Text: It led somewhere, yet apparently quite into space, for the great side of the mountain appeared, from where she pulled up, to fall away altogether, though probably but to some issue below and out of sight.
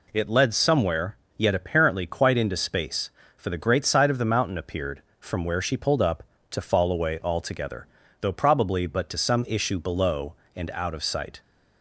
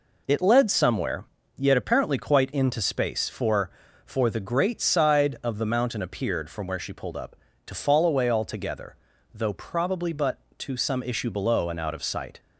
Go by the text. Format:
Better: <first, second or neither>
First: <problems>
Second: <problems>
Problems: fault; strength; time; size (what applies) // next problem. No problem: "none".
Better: first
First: none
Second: says "for" twice; at 4.0 s